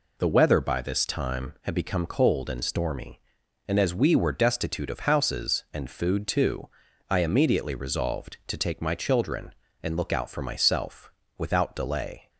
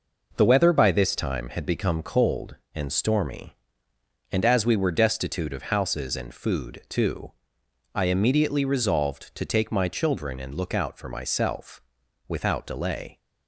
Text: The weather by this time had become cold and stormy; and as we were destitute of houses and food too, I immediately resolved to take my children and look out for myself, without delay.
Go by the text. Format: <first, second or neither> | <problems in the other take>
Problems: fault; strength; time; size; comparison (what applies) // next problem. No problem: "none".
neither | none